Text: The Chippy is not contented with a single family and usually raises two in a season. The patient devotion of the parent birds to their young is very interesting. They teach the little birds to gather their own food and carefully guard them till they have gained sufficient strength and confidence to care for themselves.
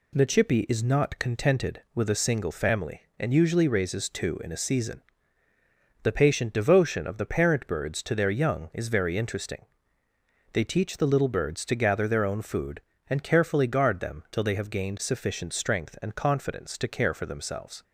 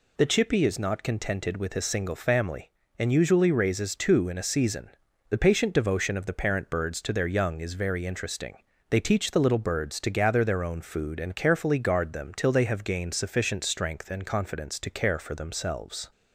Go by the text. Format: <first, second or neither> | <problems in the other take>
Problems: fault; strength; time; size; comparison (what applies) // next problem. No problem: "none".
neither | none